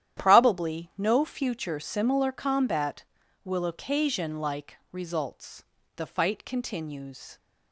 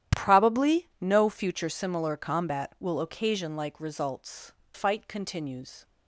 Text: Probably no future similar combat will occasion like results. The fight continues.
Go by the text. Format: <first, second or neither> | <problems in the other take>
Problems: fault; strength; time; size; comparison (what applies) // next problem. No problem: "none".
first | starts louder than the rest; strong; until 1.2 s; 11 dB; strong in the first // skips "The"; at 4.6 s